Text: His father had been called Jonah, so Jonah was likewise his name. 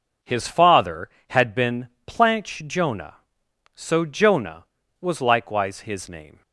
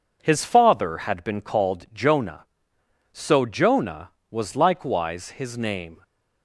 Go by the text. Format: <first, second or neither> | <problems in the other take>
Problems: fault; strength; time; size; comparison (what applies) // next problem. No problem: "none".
second | says "planch" for "called"; at 2.0 s